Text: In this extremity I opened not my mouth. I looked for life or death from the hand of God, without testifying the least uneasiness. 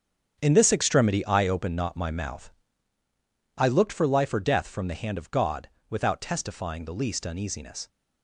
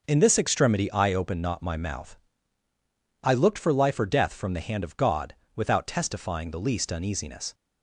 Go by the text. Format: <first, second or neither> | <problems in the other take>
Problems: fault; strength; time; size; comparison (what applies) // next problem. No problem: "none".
second | gets quieter; strong; throughout; 10.5 dB